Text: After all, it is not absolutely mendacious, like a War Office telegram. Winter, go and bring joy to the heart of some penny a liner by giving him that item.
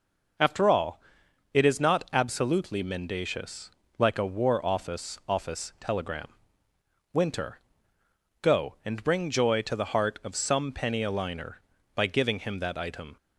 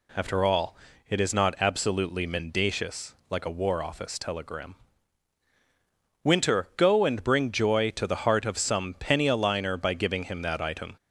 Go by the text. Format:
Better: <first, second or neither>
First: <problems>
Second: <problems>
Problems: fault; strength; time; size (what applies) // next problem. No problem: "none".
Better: second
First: says "Office" twice; at 5.2 s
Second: none